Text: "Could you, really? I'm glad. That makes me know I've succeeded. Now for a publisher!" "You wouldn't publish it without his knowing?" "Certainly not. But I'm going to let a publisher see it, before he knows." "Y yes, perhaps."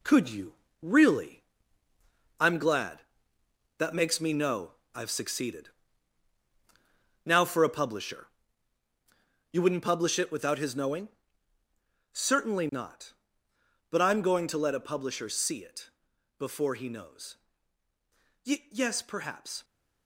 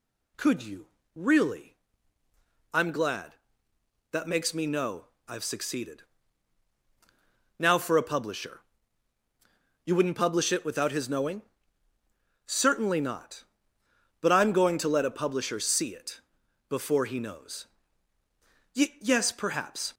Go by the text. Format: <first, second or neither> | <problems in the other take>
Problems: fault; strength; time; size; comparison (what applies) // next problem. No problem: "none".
second | gets quieter; noticeable; throughout; 5 dB // pauses between "know" and "I've"; slight; at 4.7 s; 0.24 s long; slight in the second